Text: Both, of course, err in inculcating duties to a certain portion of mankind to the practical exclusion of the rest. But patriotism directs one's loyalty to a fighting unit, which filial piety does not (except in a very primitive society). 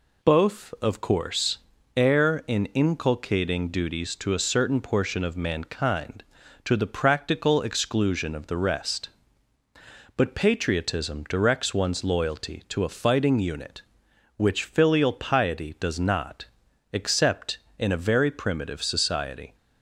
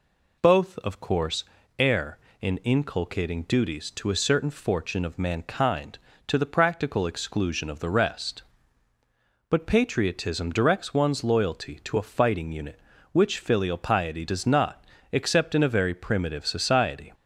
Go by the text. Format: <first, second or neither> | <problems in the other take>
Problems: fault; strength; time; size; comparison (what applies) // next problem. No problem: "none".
first | says "fortune" for "portion"; at 4.5 s